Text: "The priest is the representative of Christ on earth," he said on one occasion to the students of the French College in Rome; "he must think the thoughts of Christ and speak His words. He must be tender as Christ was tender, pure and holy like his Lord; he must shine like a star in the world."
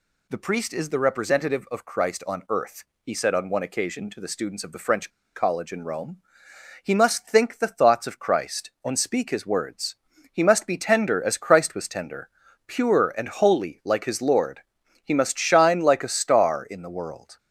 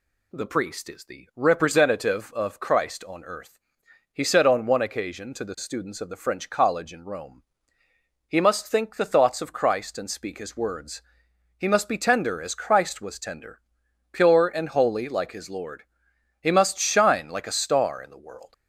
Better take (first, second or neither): second